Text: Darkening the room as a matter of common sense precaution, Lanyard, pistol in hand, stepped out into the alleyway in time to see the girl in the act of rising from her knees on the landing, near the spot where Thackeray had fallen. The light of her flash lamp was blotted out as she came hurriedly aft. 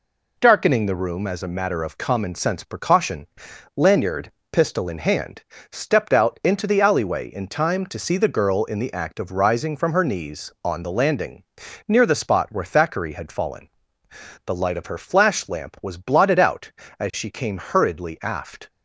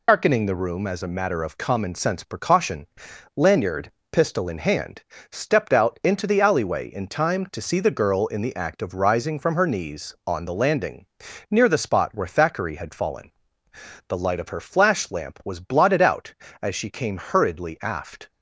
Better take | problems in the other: first | loses the start of "Darkening"; at 0.0 s; 100 ms

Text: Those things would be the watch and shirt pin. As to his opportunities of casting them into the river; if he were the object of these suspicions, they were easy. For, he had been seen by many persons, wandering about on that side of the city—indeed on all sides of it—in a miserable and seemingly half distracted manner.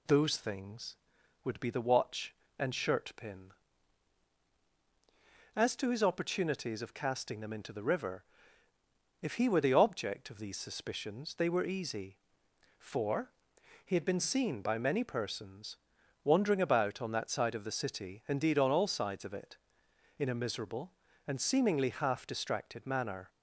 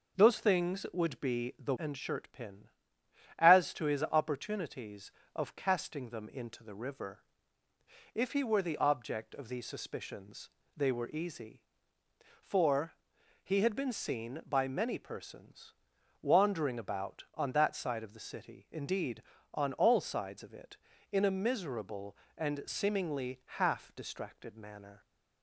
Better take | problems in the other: first | starts louder than the rest; until 1.2 s; 6.5 dB // skips "watch"; at 1.7 s

